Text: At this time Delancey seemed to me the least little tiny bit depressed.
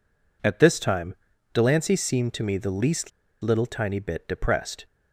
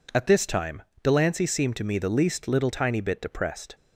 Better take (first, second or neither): second